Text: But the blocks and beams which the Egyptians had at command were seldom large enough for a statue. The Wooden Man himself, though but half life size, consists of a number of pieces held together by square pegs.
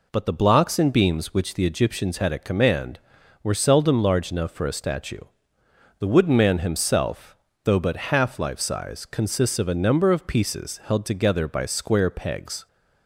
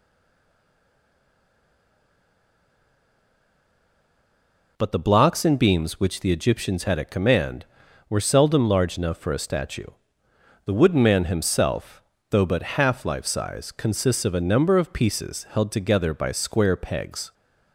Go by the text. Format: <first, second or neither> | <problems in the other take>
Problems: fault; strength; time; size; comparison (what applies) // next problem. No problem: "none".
first | stays silent before the first word; strong; until 4.7 s; 4.7 s long